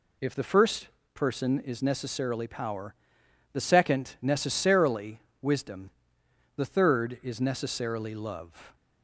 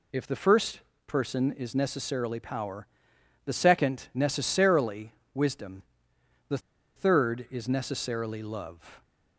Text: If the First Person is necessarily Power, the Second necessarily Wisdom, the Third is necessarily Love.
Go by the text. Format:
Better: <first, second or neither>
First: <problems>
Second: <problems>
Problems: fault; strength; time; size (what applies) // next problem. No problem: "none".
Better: first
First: pauses between "First" and "Person"; slight; at 0.8 s; 0.26 s long // pauses between "necessarily" and "Wisdom"; slight; at 5.1 s; 0.22 s long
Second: pauses between "First" and "Person"; slight; at 0.8 s; 0.26 s long // pauses between "necessarily" and "Wisdom"; slight; at 5.1 s; 0.22 s long // pauses between "the" and "Third"; at 6.5 s; 0.37 s long